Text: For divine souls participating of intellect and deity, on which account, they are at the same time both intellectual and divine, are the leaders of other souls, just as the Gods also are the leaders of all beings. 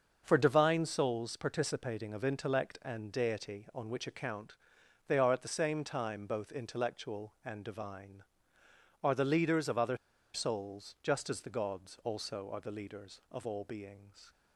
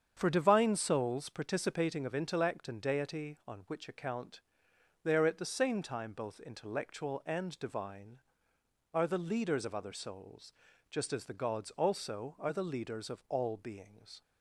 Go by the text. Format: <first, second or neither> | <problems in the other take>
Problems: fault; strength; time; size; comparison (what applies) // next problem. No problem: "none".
second | starts louder than the rest; until 1.2 s; 6.5 dB; strong in the second // pauses between "other" and "souls"; at 9.9 s; 0.37 s long